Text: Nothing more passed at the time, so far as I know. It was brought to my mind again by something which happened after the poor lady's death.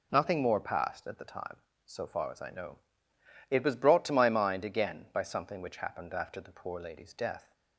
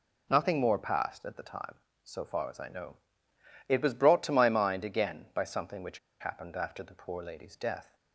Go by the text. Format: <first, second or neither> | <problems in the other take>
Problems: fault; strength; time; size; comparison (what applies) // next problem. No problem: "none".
first | pauses between "which" and "happened"; slight; at 5.9 s; 0.22 s long